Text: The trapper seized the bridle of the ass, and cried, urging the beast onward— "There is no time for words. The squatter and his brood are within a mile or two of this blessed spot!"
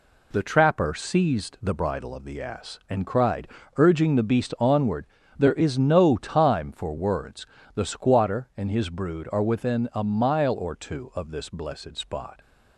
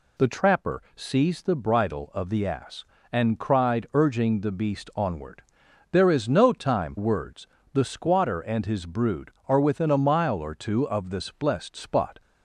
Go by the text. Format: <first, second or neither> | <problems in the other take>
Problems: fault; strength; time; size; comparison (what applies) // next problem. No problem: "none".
first | skips "for"; at 6.9 s